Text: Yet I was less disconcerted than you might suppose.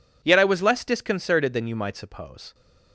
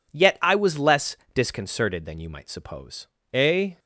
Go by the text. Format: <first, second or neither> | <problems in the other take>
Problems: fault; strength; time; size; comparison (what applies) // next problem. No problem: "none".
first | pauses between "less" and "disconcerted"; slight; at 1.1 s; 0.18 s long // goes on to say "A"; slight; from 3.3 s on; 0.44 s long